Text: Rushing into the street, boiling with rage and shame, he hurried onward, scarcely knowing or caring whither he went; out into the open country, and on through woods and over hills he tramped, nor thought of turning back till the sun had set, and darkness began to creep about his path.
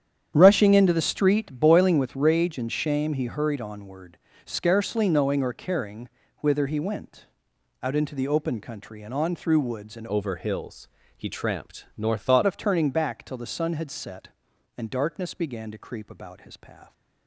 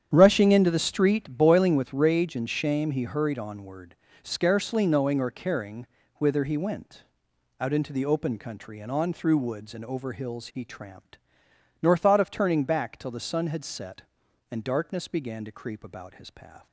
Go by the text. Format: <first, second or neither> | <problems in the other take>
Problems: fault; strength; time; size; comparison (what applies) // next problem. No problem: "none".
second | starts louder than the rest; strong; until 1.3 s; 9 dB; strong in the second // pauses between "caring" and "whither"; slight; at 6.0 s; 0.30 s long; slight in the second // changes voice from "over" to "thought"; from 10.0 to 12.4 s; 2.4 s long // pauses between "hills" and "he"; slight; at 10.8 s; 0.28 s long